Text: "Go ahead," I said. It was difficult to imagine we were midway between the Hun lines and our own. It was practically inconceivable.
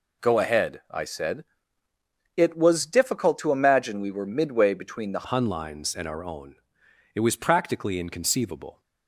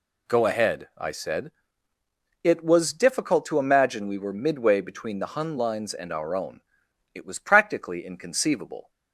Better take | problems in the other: second | changes voice at "Hun"; from 5.2 s on; 3.6 s long

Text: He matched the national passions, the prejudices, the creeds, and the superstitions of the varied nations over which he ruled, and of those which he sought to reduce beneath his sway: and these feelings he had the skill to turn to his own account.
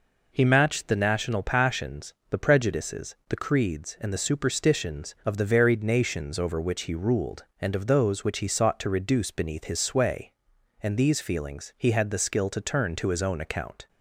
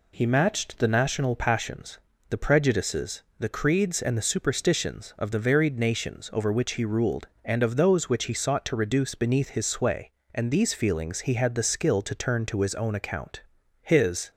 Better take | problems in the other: first | goes on to say "His"; slight; from 13.8 s on; 0.48 s long

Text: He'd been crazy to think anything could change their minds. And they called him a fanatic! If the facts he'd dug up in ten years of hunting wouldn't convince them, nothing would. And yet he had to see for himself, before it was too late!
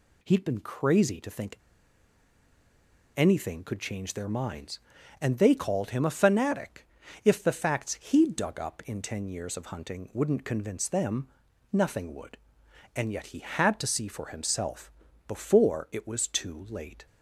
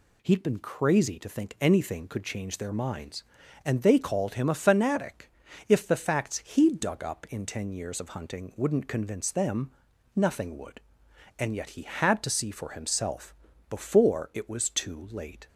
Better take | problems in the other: second | pauses between "think" and "anything"; strong; at 1.5 s; 1.5 s long

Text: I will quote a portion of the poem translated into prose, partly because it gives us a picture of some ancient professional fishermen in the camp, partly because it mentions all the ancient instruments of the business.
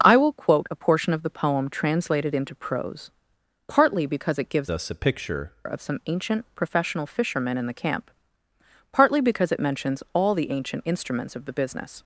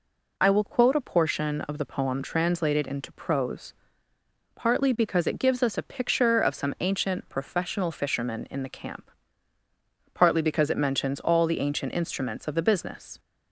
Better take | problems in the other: second | starts louder than the rest; noticeable; until 1.1 s; 6 dB // changes voice from "us" to "picture"; from 4.6 to 5.5 s; 0.9 s long

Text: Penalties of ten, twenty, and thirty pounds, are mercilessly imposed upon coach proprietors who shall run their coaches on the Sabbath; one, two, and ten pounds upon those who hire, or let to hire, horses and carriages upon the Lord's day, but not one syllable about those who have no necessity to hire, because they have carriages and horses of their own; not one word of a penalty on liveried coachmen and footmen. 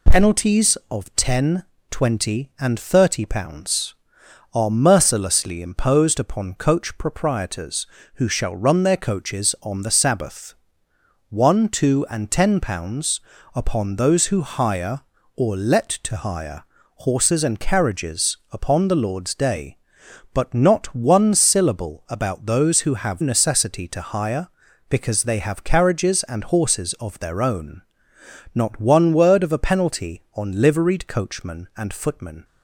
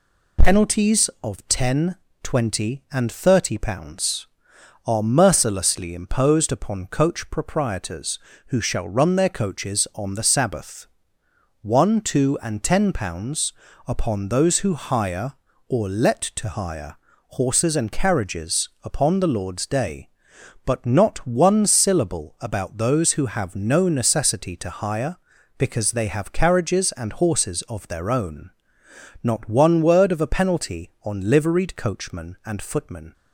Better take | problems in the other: second | pauses between "pounds" and "upon"; slight; at 13.1 s; 0.34 s long; slight in the second // skips "no"; at 23.2 s

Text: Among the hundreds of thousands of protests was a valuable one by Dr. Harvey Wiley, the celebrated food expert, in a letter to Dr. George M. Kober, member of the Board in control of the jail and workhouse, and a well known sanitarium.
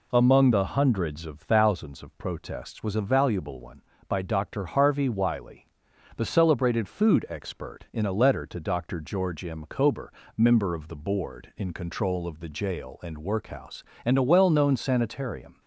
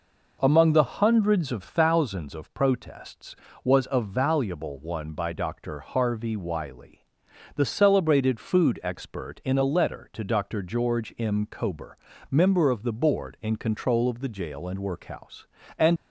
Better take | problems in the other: first | stops before "a well known sanitarium"; at 15.9 s

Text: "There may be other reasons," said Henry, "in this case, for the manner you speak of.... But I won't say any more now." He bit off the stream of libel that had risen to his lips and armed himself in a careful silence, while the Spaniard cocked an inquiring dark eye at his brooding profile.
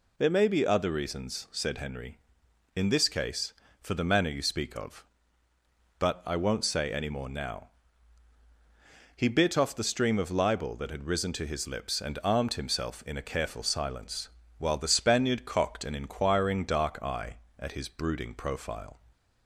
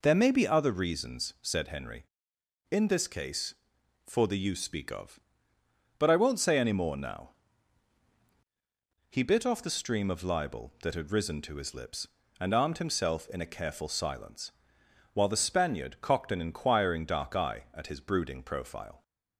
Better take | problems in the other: first | skips "manner"; at 4.3 s

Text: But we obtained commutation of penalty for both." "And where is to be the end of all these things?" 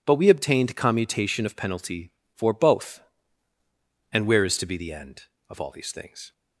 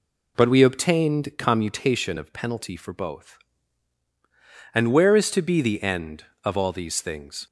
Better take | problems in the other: neither | none

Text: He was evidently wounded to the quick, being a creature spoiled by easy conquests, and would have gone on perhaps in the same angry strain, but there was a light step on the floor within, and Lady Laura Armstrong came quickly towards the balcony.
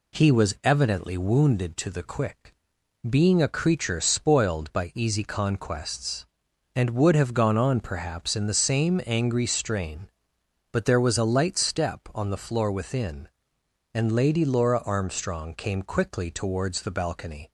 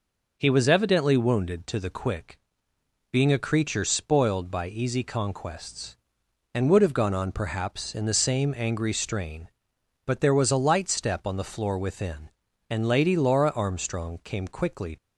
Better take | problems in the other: first | stops before "towards the balcony"; at 14.9 s

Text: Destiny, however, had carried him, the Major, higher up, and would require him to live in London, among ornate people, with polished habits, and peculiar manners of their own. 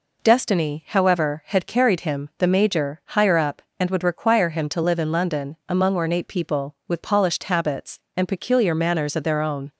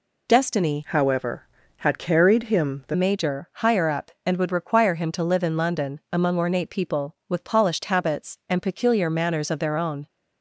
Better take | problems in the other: first | changes voice from "however" to "the"; from 0.8 to 2.9 s; 2.1 s long

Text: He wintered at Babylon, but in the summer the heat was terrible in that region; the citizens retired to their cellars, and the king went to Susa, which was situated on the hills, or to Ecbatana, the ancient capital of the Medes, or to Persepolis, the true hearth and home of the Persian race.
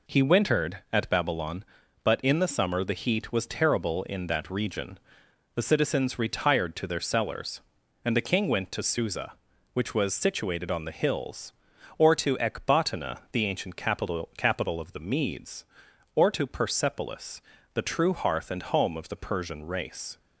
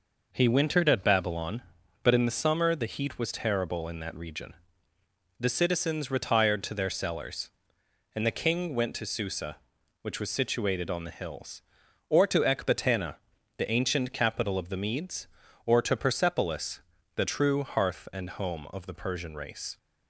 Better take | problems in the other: second | says "capital" twice; at 14.3 s

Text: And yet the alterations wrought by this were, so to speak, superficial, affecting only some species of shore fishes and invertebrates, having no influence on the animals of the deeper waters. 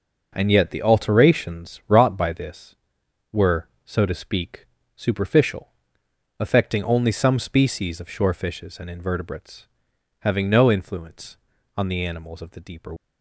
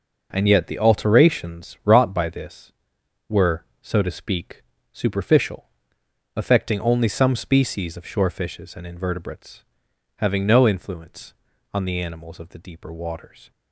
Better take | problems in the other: second | stops before "waters"; at 12.9 s

